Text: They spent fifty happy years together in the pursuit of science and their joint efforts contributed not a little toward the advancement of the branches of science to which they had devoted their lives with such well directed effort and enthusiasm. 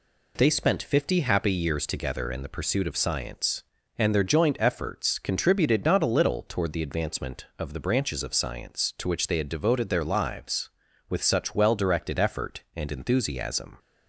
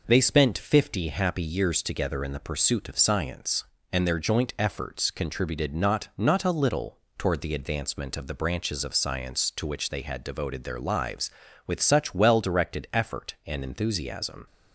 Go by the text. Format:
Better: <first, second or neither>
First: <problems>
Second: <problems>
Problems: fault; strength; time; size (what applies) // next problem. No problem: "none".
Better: first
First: none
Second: says "not" twice; at 6.1 s // pauses between "little" and "toward"; slight; at 6.9 s; 0.18 s long